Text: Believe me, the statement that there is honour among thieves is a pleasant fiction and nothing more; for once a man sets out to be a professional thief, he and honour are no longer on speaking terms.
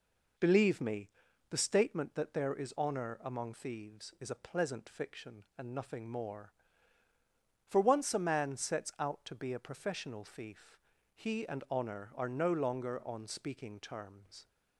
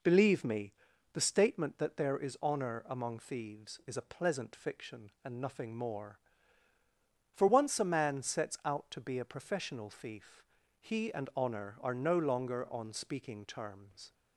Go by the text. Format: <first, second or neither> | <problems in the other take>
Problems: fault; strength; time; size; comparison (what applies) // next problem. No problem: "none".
neither | none